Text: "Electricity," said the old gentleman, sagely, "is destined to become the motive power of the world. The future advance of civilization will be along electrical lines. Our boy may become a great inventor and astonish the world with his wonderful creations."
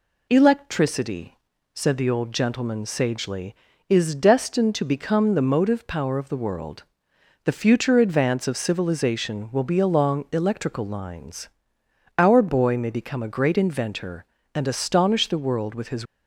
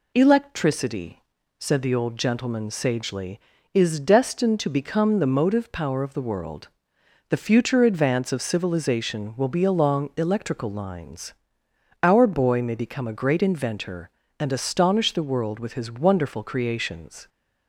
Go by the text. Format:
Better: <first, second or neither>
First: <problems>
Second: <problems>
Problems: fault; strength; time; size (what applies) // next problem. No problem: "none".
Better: second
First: stops before "wonderful creations"; at 16.0 s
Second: none